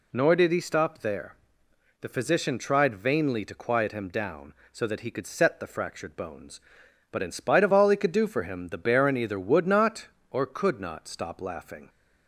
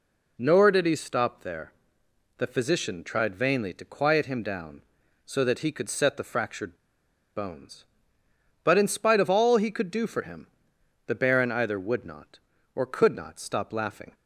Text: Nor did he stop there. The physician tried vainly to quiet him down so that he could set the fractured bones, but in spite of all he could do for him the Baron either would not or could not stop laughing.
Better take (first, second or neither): first